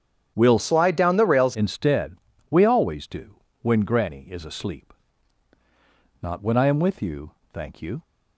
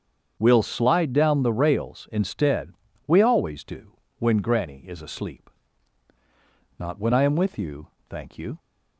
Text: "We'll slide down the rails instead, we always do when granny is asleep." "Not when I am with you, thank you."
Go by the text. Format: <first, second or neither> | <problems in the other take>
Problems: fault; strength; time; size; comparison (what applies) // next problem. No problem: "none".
second | starts louder than the rest; strong; until 1.3 s; 9 dB; strong in the second // changes voice from "slide" to "rails"; from 0.5 to 1.5 s; 1.0 s long // pauses between "do" and "when"; slight; at 3.3 s; 0.26 s long; slight in the second